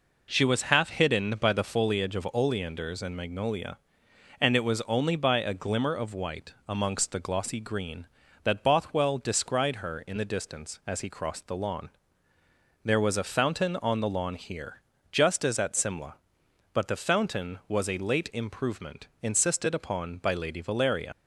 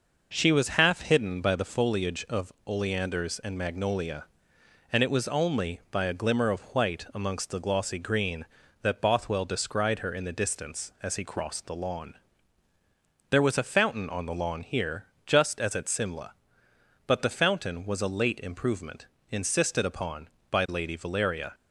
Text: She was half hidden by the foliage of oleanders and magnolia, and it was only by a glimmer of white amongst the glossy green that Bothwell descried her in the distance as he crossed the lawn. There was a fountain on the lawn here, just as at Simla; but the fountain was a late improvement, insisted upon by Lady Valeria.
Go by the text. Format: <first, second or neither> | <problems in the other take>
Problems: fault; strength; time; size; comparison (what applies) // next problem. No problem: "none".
second | leaves "Valeria" unfinished; at 21.1 s; 70 ms